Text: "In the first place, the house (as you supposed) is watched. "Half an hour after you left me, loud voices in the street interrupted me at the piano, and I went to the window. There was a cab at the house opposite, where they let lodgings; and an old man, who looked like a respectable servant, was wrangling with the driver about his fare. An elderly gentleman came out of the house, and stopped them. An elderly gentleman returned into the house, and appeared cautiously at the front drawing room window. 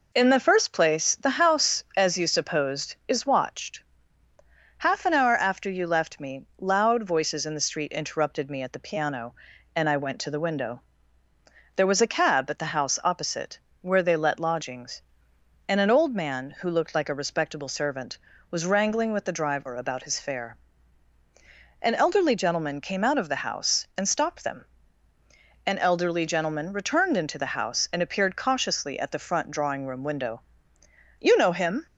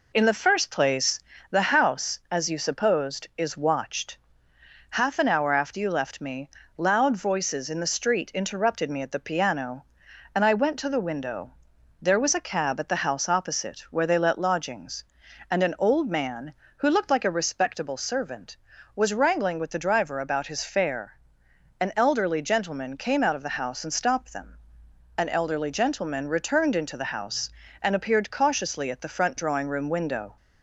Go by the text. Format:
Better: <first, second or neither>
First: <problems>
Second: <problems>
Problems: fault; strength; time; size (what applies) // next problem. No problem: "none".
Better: second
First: goes on to say "You know him"; noticeable; from 31.2 s on; 0.66 s long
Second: none